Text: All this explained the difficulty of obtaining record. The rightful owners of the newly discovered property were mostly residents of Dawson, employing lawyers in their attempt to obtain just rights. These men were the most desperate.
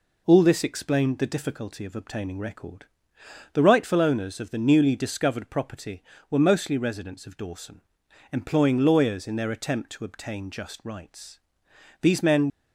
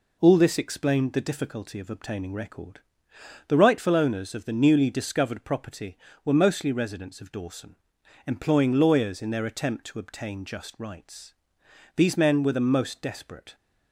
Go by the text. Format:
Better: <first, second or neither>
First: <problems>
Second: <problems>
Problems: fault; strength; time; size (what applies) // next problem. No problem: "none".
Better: second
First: stops before "were the most desperate"; at 12.4 s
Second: none